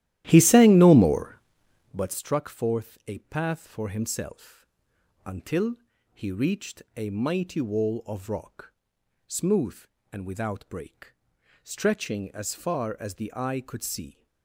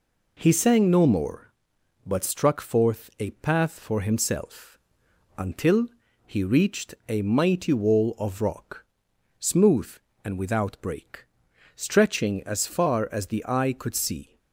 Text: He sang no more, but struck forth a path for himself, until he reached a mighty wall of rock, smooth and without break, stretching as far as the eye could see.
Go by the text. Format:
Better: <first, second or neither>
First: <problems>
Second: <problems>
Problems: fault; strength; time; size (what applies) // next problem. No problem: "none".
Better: second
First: starts louder than the rest; strong; until 2.1 s; 13.5 dB // pauses between "until" and "he"; at 5.7 s; 0.40 s long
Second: pauses between "until" and "he"; at 5.8 s; 0.40 s long